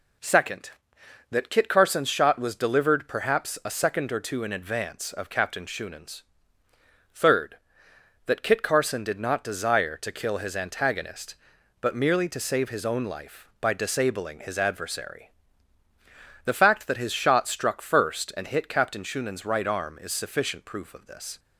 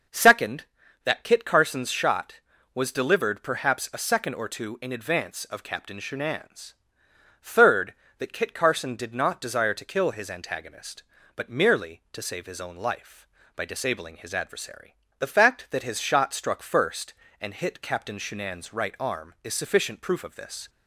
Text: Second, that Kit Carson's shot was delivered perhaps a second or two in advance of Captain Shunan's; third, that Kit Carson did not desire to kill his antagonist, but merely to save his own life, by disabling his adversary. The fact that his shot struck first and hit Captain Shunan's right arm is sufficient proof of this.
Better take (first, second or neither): neither